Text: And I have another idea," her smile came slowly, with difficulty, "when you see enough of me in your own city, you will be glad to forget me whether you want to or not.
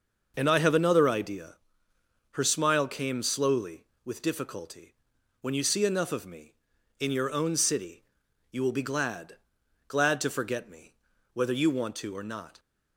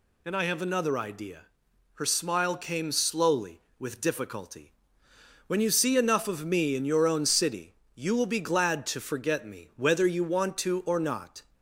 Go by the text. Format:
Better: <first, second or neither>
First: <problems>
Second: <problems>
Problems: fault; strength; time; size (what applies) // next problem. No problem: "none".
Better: second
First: starts louder than the rest; noticeable; until 1.3 s; 6 dB // says "glad" twice; at 9.8 s // pauses between "me" and "whether"; at 10.9 s; 0.40 s long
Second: none